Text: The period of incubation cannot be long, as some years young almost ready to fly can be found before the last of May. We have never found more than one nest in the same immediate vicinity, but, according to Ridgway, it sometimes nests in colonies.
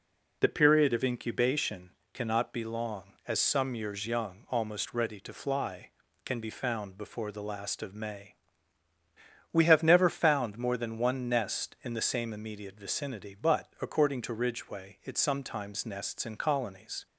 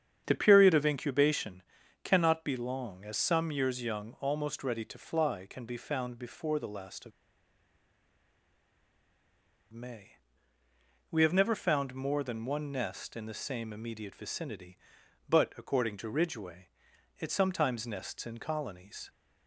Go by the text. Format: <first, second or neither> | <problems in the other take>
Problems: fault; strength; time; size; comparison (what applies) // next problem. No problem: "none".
first | starts louder than the rest; strong; until 1.2 s; 8 dB // pauses between "incubation" and "cannot"; at 1.6 s; 0.40 s long; slight in the first // pauses between "of" and "May"; strong; at 7.1 s; 2.6 s long